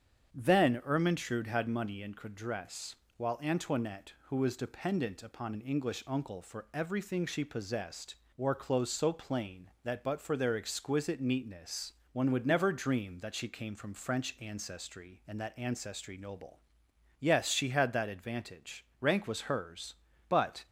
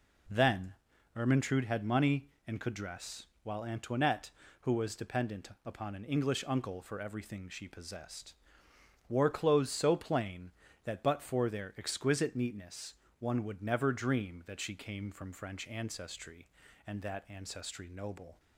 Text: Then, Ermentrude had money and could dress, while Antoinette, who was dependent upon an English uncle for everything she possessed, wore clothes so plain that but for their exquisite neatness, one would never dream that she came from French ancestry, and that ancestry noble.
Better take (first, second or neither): second